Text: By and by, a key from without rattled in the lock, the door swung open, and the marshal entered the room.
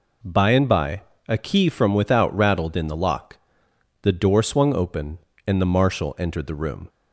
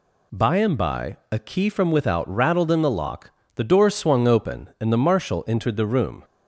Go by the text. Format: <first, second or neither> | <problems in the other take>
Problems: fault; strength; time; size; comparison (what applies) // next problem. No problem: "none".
neither | none